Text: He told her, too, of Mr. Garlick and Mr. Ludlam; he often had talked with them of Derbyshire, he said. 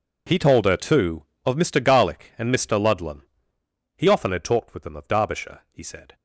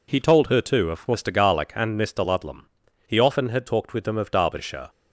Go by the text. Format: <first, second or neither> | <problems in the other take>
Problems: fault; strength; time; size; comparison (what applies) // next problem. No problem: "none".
first | stops before "he said"; at 4.8 s